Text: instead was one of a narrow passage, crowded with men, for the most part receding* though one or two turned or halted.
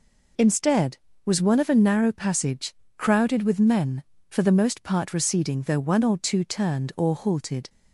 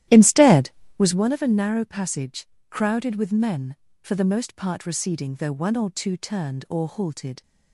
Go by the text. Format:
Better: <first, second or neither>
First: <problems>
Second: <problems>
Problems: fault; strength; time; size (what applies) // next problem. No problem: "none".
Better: first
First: none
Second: starts louder than the rest; strong; until 1.3 s; 13 dB